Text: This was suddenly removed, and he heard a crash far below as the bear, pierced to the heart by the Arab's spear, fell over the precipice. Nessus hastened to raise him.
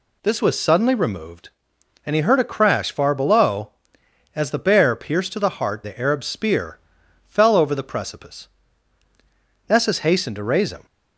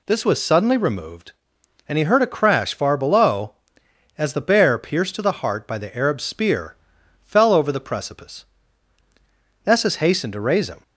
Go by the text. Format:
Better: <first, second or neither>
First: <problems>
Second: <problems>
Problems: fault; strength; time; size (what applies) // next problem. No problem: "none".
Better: second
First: skips "by"; at 5.8 s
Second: none